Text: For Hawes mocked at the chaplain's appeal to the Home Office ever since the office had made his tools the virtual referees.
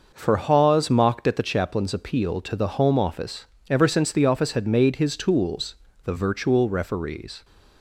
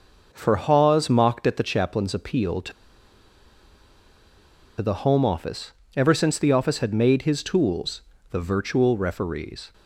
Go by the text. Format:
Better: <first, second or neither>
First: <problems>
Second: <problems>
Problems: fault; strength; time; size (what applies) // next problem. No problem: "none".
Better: first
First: starts louder than the rest; noticeable; until 1.1 s; 6 dB // pauses between "Office" and "ever"; slight; at 3.4 s; 0.24 s long // pauses between "tools" and "the"; slight; at 5.7 s; 0.28 s long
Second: starts louder than the rest; noticeable; until 1.3 s; 6 dB // pauses between "to" and "the"; strong; at 2.7 s; 2.0 s long // pauses between "Office" and "ever"; slight; at 5.7 s; 0.24 s long // pauses between "tools" and "the"; slight; at 8.0 s; 0.28 s long